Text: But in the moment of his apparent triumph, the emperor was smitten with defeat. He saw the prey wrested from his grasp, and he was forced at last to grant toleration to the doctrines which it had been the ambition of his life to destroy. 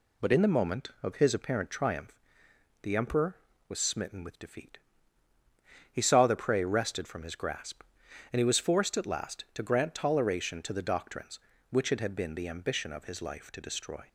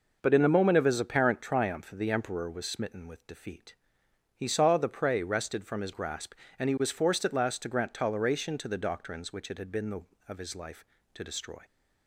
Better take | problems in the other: first | skips "ambition"; at 10.1 s

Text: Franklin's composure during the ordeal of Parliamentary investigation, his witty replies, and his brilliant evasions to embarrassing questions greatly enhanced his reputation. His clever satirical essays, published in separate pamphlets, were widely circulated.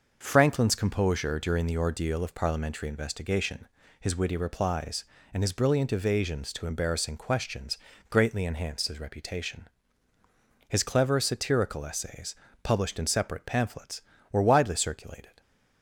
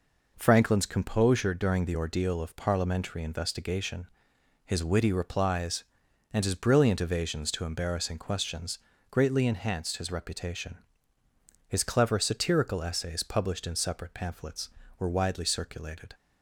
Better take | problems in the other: neither | pauses between "questions" and "greatly"; slight; the same in both

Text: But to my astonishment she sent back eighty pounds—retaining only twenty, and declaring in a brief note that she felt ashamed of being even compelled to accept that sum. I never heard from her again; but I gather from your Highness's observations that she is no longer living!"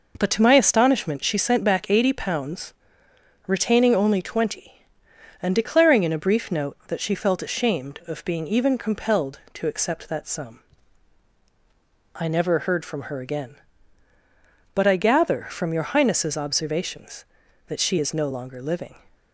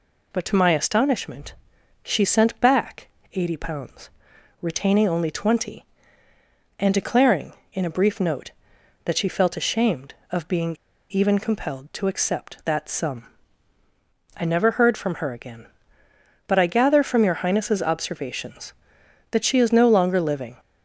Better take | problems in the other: first | pauses between "astonishment" and "she"; noticeable; at 1.5 s; 0.48 s long // pauses between "back" and "eighty"; slight; at 3.0 s; 0.24 s long // pauses between "being" and "even"; slight; at 10.7 s; 0.35 s long

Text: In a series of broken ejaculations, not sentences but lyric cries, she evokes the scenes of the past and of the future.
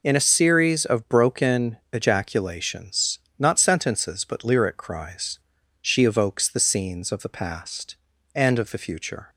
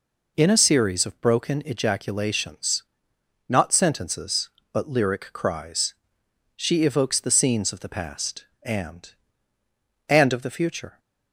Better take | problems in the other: first | says "and" twice; at 10.0 s

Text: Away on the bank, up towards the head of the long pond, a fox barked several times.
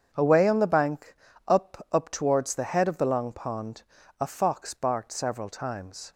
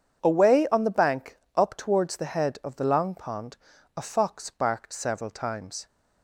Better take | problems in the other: second | starts louder than the rest; strong; until 1.1 s; 7.5 dB; strong in the second // says "up" twice; at 1.8 s

